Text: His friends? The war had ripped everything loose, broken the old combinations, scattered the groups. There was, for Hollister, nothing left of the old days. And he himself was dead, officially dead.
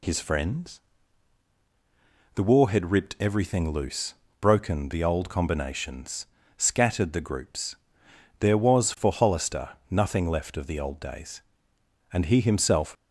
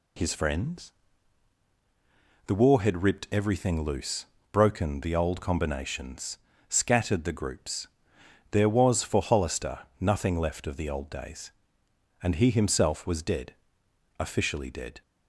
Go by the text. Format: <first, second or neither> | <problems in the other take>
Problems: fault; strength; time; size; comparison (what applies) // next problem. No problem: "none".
second | stops before "was dead officially dead"; at 12.9 s